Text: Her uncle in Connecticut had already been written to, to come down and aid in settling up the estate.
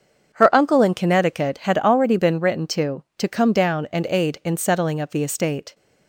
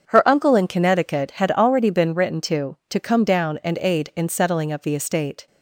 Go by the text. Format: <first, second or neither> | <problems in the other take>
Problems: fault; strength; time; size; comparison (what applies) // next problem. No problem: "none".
neither | starts louder than the rest; the same in both